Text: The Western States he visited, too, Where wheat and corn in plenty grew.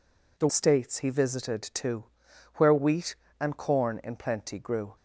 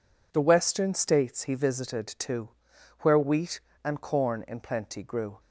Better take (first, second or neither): second